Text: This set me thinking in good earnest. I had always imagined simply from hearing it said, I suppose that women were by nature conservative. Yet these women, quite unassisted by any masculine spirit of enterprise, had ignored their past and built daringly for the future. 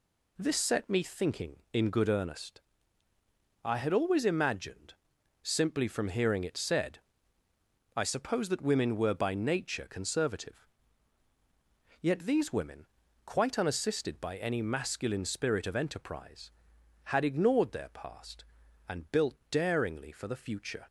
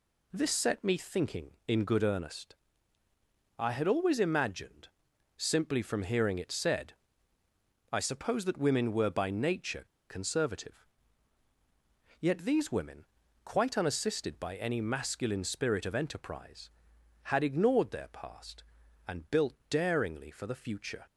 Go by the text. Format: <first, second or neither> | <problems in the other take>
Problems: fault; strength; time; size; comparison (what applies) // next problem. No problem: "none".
first | pauses between "imagined" and "simply"; noticeable; at 4.8 s; 0.48 s long; noticeable in the first // pauses between "nature" and "conservative"; slight; at 9.8 s; 0.27 s long // pauses between "built" and "daringly"; slight; at 19.5 s; 0.16 s long; slight in the first